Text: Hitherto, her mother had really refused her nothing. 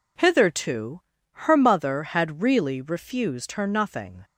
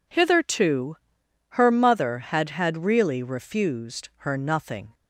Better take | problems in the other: first | says "had" twice; at 2.4 s

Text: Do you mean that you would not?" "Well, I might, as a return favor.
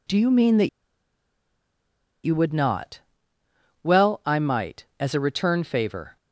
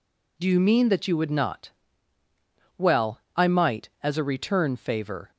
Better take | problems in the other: second | pauses between "that" and "you"; strong; at 0.6 s; 1.5 s long

